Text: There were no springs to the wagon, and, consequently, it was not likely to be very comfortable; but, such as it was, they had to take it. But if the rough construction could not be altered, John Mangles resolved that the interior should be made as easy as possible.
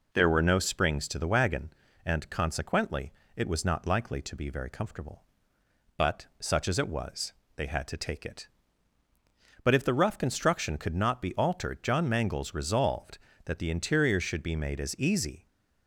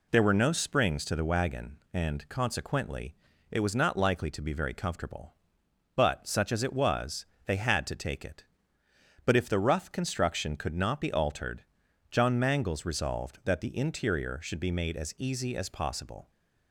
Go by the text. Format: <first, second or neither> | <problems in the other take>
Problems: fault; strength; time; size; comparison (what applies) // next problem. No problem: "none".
second | stops before "as possible"; at 15.4 s